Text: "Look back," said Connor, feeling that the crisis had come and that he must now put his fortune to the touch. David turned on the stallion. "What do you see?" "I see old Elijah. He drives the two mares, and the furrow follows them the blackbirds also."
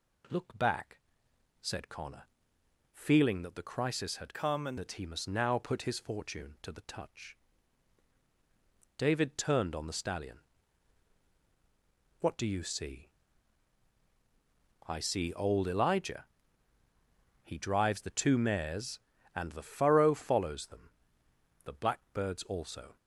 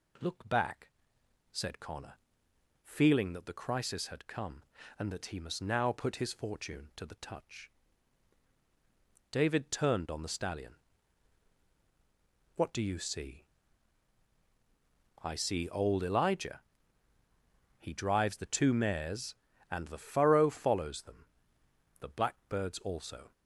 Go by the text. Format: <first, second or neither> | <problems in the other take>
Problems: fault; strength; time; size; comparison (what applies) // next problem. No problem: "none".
second | changes voice from "come" to "and"; from 4.3 to 4.7 s; 0.4 s long // pauses between "them" and "the"; noticeable; at 20.9 s; 0.74 s long; noticeable in the second